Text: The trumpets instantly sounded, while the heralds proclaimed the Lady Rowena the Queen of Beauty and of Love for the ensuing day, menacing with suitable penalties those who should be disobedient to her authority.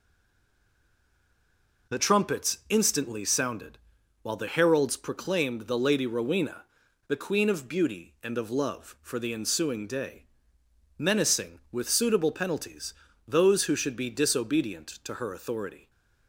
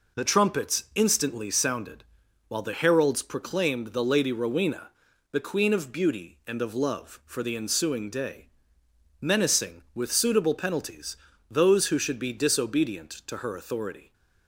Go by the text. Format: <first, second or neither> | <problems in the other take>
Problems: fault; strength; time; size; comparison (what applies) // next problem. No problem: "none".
second | stays silent before the first word; noticeable; until 1.8 s; 1.8 s long // pauses between "Rowena" and "the"; at 6.6 s; 0.43 s long; also in the second // pauses between "penalties" and "those"; slight; at 12.9 s; 0.32 s long; slight in the second